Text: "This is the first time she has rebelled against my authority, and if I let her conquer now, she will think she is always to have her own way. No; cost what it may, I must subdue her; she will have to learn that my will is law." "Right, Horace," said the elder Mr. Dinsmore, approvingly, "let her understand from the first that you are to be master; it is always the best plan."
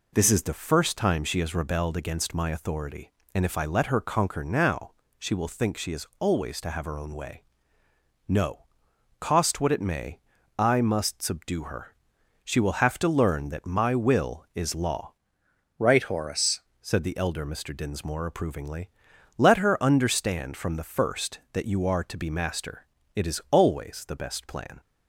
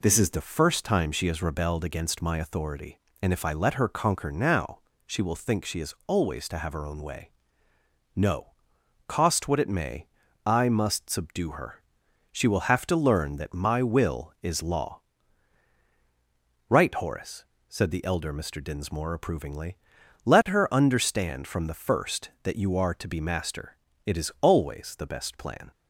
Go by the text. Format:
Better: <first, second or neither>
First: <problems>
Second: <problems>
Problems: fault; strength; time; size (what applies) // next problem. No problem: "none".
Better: second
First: changes voice from "Right" to "Horace"; from 15.7 to 16.6 s; 0.9 s long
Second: none